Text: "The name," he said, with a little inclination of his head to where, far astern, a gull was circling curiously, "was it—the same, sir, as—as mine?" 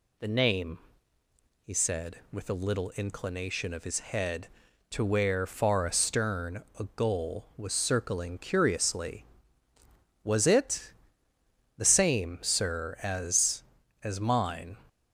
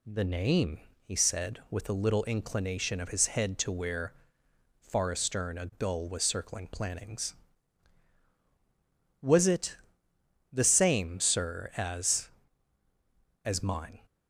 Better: first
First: none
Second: says "plannings" for "curiously"; at 6.6 s

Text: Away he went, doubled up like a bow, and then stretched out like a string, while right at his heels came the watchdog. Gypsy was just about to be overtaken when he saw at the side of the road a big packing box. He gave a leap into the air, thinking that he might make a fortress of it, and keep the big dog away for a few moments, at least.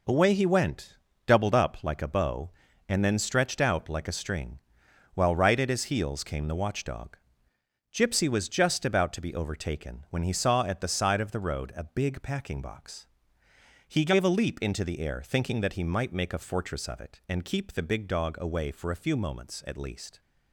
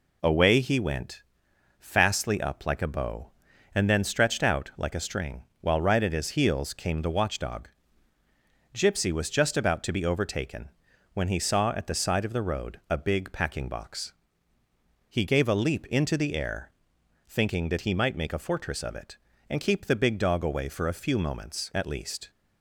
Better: first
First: none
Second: says "fastly" for "doubled"; at 1.7 s // pauses between "overtaken" and "when"; at 10.6 s; 0.44 s long

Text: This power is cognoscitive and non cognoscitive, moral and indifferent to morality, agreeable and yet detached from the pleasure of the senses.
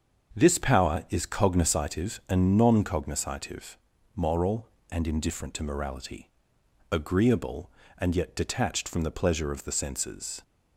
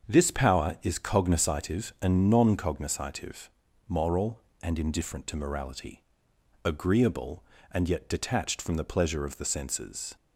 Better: neither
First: starts louder than the rest; until 1.4 s; 7 dB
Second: starts louder than the rest; until 1.1 s; 7 dB

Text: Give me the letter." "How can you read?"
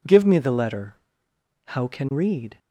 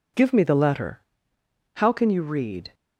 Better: second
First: skips "you"; at 2.1 s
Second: none

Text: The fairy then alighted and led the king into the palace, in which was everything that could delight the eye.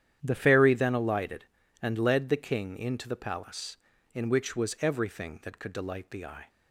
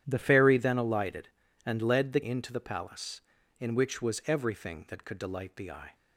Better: first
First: starts louder than the rest; strong; until 1.2 s; 10 dB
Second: starts louder than the rest; strong; until 1.0 s; 10 dB // skips "king"; at 2.2 s

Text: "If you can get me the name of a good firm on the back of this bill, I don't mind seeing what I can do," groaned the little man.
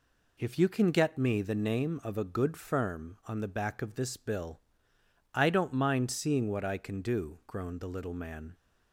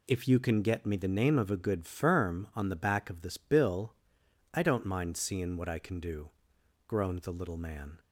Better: neither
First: none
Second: none

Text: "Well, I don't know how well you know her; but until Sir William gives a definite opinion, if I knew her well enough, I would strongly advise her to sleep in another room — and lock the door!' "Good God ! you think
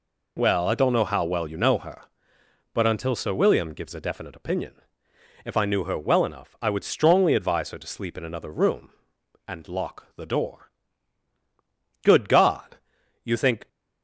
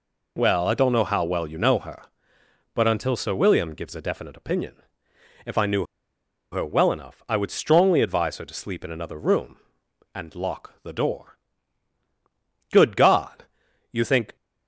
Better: first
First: none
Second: pauses between "knew" and "her"; noticeable; at 5.8 s; 0.66 s long

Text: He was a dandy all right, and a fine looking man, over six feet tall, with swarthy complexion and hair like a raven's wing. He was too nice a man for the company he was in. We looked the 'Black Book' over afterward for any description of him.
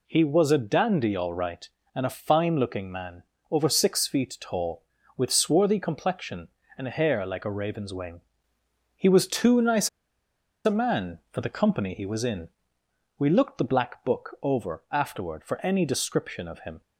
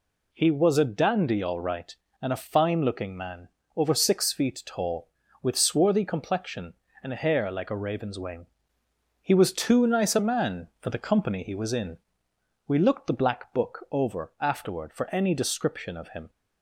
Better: second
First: pauses between "nice" and "a"; noticeable; at 9.8 s; 0.76 s long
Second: none

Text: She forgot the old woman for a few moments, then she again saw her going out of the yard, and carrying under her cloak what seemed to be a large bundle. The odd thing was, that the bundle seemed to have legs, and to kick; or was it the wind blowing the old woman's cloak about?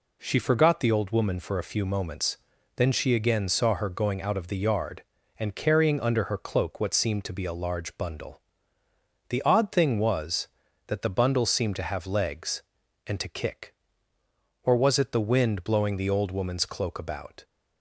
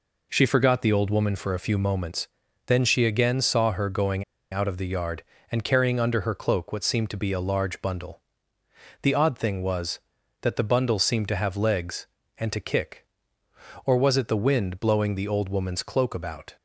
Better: first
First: none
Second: pauses between "going" and "out"; slight; at 4.2 s; 0.29 s long

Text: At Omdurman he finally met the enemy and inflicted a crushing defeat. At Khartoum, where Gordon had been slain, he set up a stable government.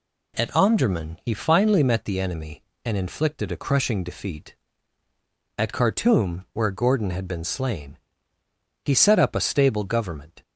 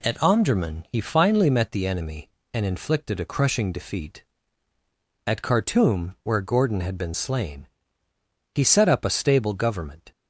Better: neither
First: none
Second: none

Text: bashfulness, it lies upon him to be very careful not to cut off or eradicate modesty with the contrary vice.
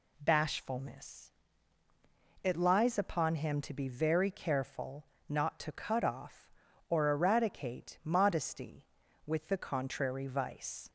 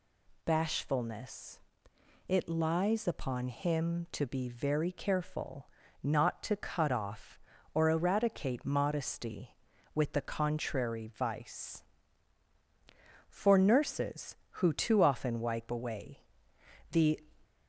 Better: first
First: pauses between "careful" and "not"; slight; at 5.0 s; 0.22 s long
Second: pauses between "careful" and "not"; slight; at 5.6 s; 0.34 s long // goes on to say "For nurses who too often wipe away the"; strong; from 13.2 s on; 3.9 s long

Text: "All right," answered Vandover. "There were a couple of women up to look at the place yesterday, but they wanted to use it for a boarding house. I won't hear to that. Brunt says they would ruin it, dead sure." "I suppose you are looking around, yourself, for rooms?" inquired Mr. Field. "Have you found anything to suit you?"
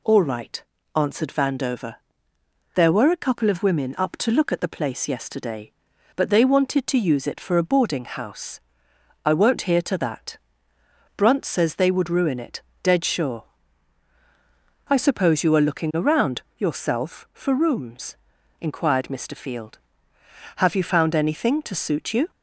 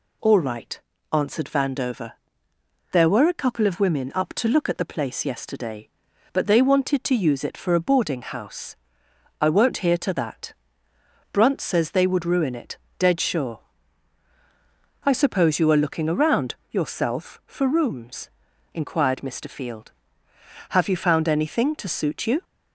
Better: neither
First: none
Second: none

